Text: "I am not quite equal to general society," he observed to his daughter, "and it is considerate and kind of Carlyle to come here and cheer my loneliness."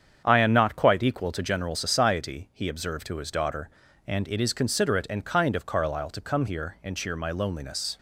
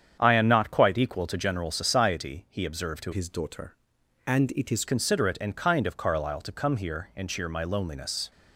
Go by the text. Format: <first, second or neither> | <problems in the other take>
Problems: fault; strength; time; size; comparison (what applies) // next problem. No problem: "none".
first | starts louder than the rest; strong; until 1.2 s; 8.5 dB; strong in the first // changes voice from "his" to "is"; from 3.1 to 4.8 s; 1.7 s long